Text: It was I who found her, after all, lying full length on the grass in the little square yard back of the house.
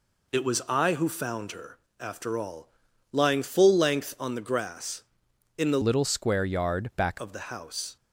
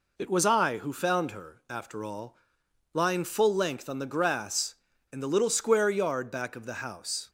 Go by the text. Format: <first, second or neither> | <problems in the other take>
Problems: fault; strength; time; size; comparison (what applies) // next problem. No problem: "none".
second | changes voice from "little" to "back"; from 5.8 to 7.1 s; 1.3 s long